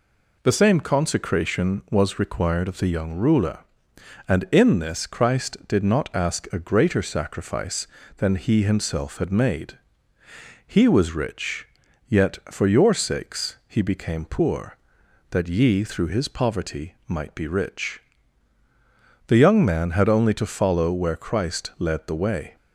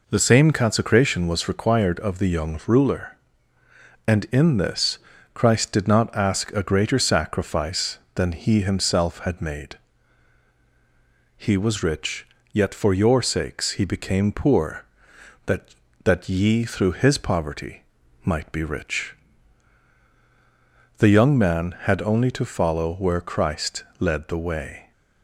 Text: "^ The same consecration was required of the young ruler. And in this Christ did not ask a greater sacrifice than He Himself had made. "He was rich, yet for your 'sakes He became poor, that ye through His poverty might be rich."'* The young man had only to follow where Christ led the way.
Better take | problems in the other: first | pauses between "this" and "Christ"; slight; at 4.9 s; 0.34 s long // says "that" twice; at 16.0 s // pauses between "poverty" and "might"; at 17.8 s; 0.40 s long // pauses between "Christ" and "led"; slight; at 23.8 s; 0.16 s long

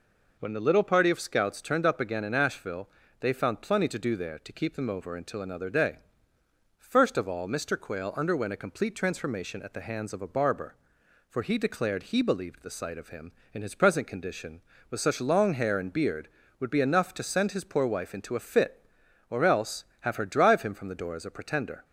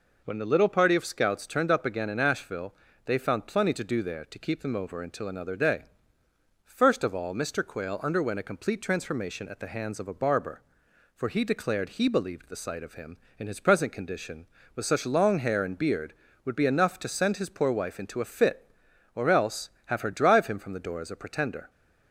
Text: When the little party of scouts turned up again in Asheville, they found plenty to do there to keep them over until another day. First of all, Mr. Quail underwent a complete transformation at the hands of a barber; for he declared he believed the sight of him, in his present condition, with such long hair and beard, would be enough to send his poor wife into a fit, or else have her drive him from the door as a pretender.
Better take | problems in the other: neither | none

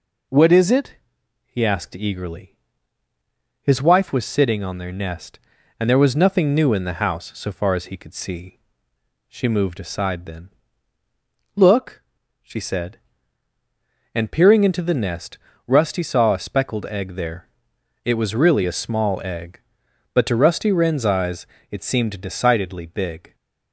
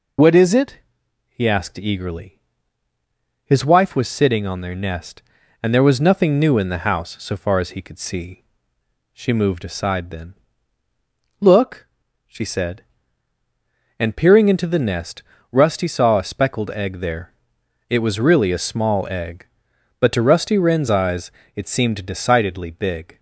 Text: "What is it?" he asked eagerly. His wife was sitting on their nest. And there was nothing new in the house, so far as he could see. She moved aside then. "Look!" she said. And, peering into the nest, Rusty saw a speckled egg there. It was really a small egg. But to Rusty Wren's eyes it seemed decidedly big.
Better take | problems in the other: first | loses the start of "What"; at 0.1 s; 55 ms // pauses between "eyes" and "it"; slight; at 21.2 s; 0.26 s long; slight in the first

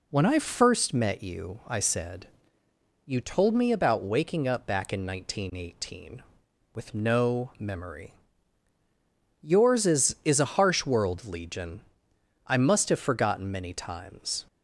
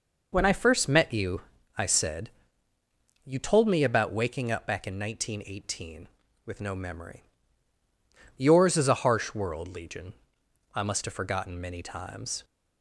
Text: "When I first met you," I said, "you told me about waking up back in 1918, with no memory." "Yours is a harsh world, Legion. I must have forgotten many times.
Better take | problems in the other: second | says "is" twice; at 10.2 s

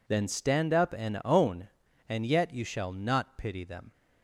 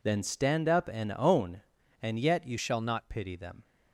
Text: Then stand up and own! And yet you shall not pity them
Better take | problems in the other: first | changes voice from "shall" to "not"; from 2.5 to 3.1 s; 0.6 s long

